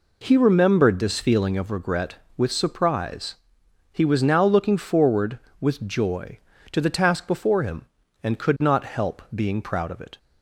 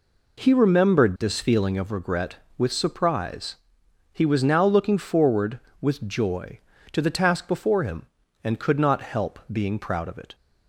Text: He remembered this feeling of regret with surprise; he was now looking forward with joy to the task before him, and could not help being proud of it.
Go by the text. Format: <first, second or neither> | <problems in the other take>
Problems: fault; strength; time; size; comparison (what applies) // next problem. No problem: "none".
neither | none